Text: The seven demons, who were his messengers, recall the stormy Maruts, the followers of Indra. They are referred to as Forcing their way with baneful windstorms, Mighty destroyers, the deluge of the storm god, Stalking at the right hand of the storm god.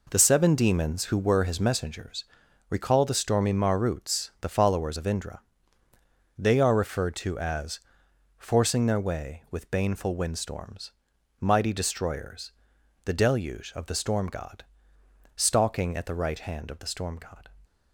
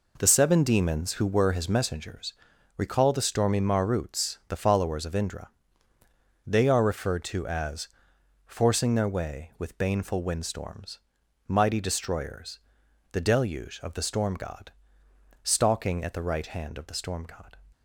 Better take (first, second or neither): neither